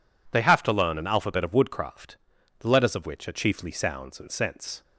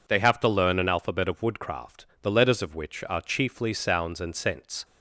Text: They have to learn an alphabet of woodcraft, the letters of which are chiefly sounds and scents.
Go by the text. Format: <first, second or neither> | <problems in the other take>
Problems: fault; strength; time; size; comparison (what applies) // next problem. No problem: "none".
neither | none